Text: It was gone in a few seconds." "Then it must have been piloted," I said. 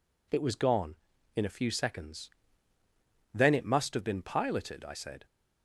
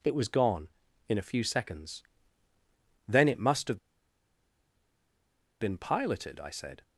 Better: first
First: none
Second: pauses between "have" and "been"; strong; at 3.7 s; 1.8 s long

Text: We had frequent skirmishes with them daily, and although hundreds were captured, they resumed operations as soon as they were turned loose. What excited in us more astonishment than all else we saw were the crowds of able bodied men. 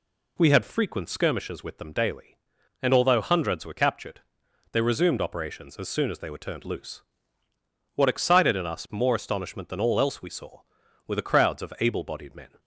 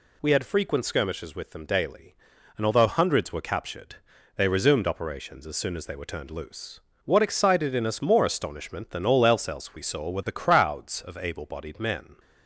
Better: first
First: none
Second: says "else" twice; at 9.4 s

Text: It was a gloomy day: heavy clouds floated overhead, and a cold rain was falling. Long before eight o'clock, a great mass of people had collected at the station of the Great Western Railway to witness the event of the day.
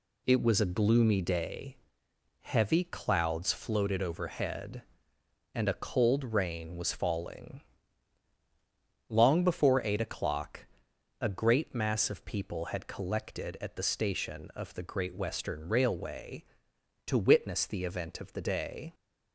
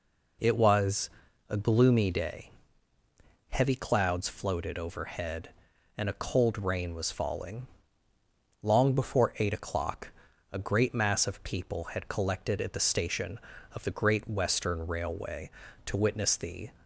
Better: first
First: none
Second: pauses between "was" and "a"; at 1.0 s; 0.40 s long // stops before "event of the day"; at 16.8 s

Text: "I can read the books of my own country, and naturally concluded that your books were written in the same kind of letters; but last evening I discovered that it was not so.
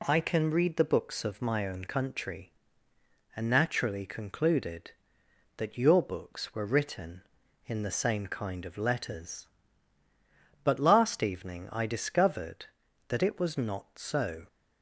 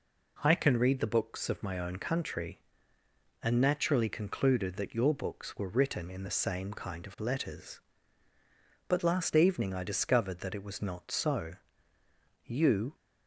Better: first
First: none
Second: goes on to say "You"; from 12.4 s on; 0.50 s long

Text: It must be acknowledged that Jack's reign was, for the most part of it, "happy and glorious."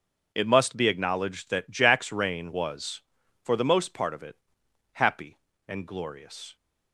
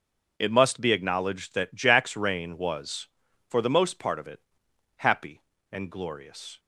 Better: neither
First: none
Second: none

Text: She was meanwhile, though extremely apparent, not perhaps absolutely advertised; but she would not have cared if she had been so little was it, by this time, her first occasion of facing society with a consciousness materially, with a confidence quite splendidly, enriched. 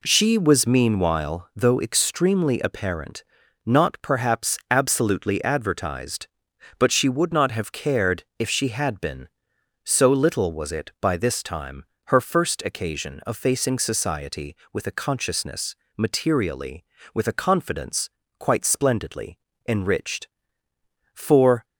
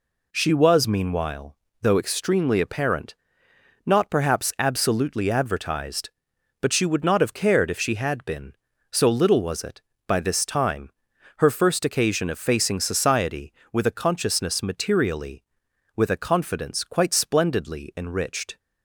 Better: second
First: pauses between "consciousness" and "materially"; slight; at 15.7 s; 0.22 s long // pauses between "confidence" and "quite"; slight; at 18.0 s; 0.30 s long // goes on to say "For"; from 21.1 s on; 0.52 s long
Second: none

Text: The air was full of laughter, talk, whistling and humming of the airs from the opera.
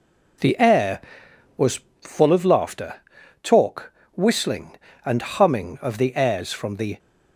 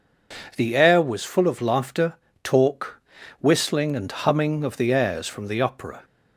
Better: second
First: pauses between "was" and "full"; slight; at 1.7 s; 0.22 s long // stops before "opera"; at 6.9 s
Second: none

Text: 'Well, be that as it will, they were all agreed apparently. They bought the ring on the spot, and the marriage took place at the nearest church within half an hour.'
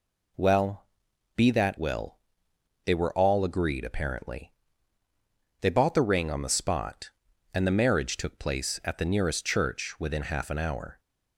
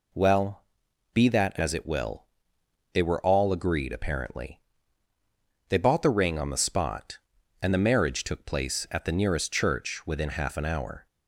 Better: second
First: skips "as it"; at 1.7 s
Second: none

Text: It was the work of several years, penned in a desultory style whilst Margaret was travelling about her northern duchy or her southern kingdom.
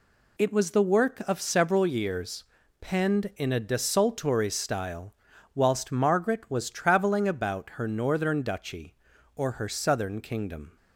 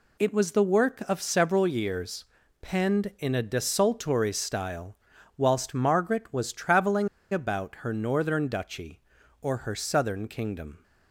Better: first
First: pauses between "style" and "whilst"; at 5.1 s; 0.42 s long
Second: pauses between "style" and "whilst"; at 4.9 s; 0.42 s long // pauses between "travelling" and "about"; slight; at 7.0 s; 0.23 s long

